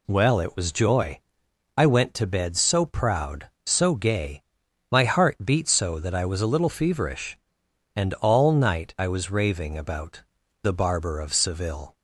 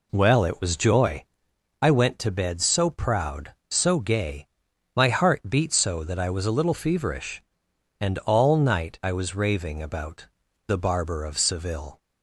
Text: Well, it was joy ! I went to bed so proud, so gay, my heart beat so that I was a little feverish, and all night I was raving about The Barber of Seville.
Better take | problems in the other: first | starts louder than the rest; slight; until 1.4 s; 3 dB // pauses between "about" and "The"; at 10.2 s; 0.40 s long; also in the first

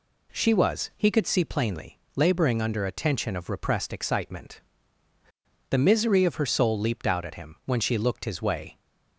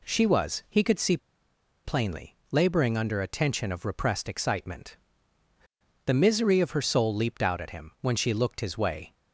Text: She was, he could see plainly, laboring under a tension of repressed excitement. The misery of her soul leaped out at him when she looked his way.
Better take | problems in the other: first | pauses between "see" and "plainly"; noticeable; at 1.1 s; 0.67 s long

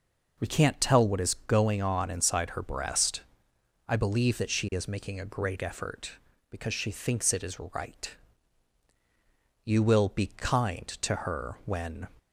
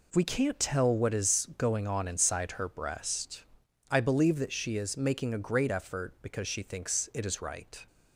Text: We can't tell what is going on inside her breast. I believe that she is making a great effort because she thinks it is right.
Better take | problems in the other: second | goes on to say "You will be kind to her when"; strong; from 9.6 s on; 2.4 s long

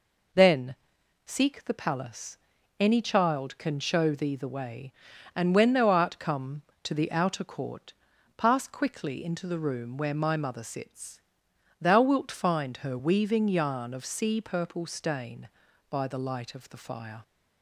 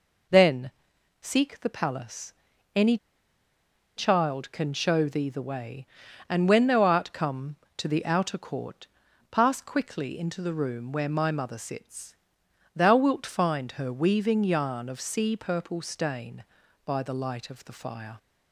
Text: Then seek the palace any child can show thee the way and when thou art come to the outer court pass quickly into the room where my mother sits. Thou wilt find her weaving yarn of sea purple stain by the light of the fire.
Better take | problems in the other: first | pauses between "Then" and "seek"; noticeable; at 0.7 s; 0.50 s long; noticeable in the first // pauses between "palace" and "any"; at 2.3 s; 0.42 s long; also in the first // pauses between "any" and "child"; at 2.9 s; 1.0 s long // pauses between "court" and "pass"; at 8.8 s; 0.44 s long; also in the first

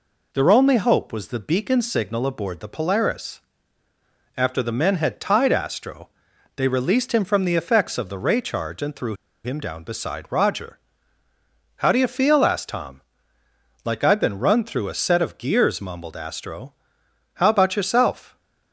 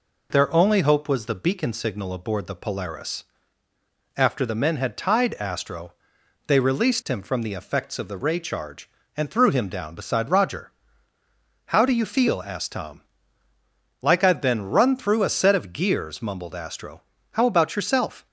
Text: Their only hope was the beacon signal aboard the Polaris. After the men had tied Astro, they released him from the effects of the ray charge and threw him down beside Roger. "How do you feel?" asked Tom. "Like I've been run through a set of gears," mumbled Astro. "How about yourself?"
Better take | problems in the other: second | pauses between "threw" and "him"; slight; at 9.1 s; 0.31 s long

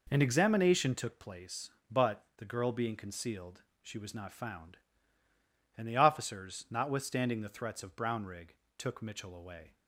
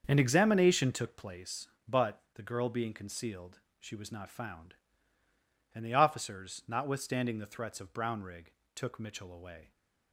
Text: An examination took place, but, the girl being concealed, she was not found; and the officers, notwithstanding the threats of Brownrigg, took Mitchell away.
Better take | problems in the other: first | starts louder than the rest; until 1.7 s; 6.5 dB

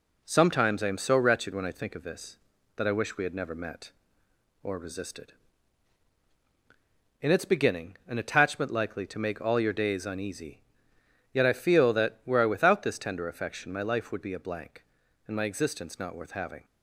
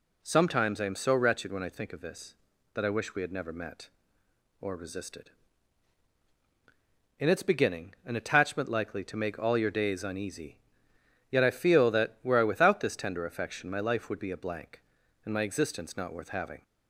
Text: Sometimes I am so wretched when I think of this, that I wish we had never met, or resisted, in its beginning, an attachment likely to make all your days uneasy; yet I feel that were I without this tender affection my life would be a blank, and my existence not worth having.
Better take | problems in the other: second | gets quieter; throughout; 3.5 dB

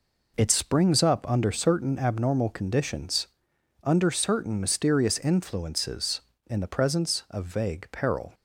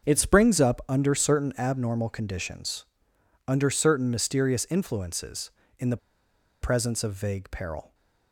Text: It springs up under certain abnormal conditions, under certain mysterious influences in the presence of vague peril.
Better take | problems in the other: first | starts louder than the rest; until 1.1 s; 6.5 dB // pauses between "the" and "presence"; noticeable; at 5.9 s; 0.64 s long // stays silent after the last word; slight; from 7.8 s on; 0.5 s long

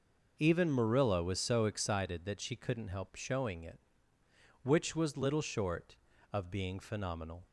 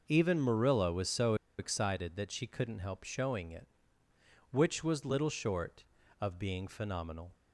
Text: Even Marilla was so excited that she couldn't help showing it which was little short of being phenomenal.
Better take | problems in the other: first | pauses between "so" and "excited"; slight; at 1.3 s; 0.24 s long

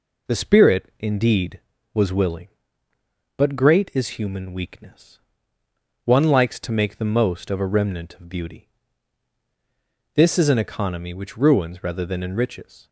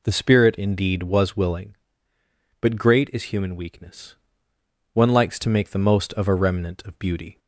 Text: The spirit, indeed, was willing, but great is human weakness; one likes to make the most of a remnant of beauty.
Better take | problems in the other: second | goes on to say "This is an economy which ruins rather than enriches"; strong; from 10.1 s on; 2.7 s long

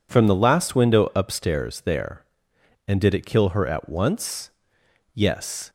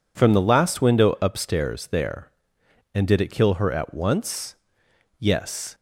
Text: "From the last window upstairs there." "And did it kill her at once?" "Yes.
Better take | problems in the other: neither | none

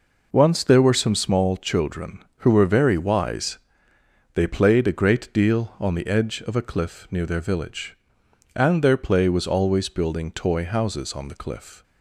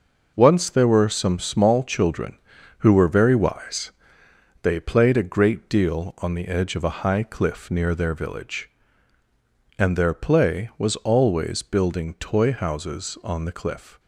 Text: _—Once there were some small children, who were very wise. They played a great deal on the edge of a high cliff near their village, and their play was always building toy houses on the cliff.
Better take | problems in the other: second | skips "high"; at 6.6 s

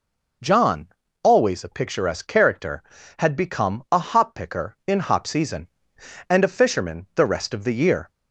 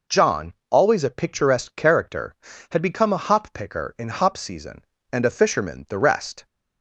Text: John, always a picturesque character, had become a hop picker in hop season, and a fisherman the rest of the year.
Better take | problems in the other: first | stops before "of the year"; at 6.4 s

